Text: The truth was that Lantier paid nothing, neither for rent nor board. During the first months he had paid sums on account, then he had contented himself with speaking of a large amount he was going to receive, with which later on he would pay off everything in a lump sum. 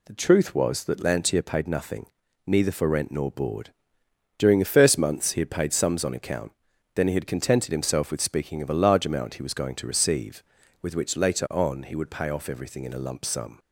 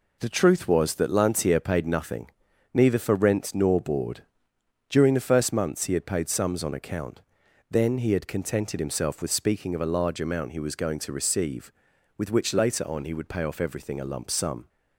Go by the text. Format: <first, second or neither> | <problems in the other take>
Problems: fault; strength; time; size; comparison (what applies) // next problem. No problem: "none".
first | skips "in"; at 14.0 s